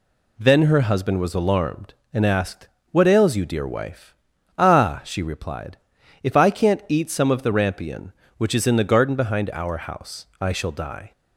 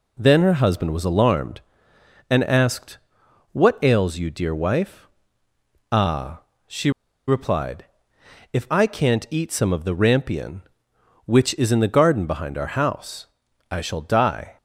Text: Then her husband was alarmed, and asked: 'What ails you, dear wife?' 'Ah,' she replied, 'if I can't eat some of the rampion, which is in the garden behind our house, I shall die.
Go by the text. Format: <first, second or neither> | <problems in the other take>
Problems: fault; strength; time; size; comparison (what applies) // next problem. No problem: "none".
first | pauses between "she" and "replied"; at 6.8 s; 0.37 s long